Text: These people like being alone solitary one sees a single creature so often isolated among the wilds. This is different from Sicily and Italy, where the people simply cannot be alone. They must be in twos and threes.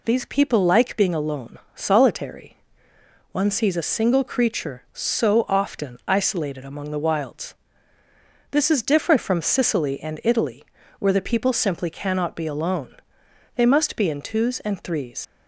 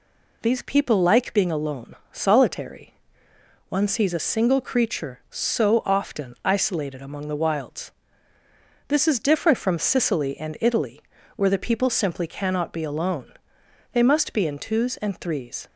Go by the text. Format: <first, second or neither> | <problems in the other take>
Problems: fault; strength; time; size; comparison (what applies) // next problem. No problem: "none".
second | pauses between "alone" and "solitary"; slight; at 1.5 s; 0.16 s long; slight in the second // pauses between "solitary" and "one"; noticeable; at 2.5 s; 0.74 s long; noticeable in the second // leaves "threes" unfinished; at 15.2 s; 40 ms